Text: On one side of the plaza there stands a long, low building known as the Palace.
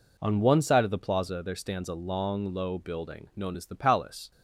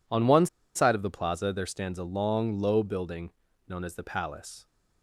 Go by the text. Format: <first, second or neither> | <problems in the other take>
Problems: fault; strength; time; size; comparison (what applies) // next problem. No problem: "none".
first | pauses between "one" and "side"; slight; at 0.4 s; 0.29 s long // pauses between "building" and "known"; at 3.3 s; 0.38 s long